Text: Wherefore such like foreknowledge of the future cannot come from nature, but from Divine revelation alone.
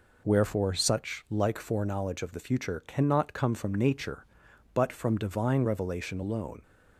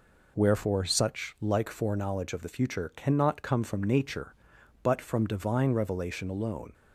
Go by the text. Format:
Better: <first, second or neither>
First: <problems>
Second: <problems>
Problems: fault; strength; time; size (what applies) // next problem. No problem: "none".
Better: neither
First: none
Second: none